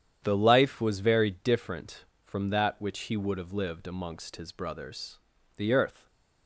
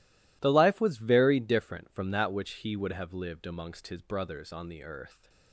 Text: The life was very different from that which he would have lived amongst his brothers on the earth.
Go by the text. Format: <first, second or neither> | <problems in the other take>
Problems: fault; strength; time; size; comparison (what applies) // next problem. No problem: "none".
second | starts louder than the rest; strong; until 1.2 s; 9.5 dB // skips "on"; at 5.3 s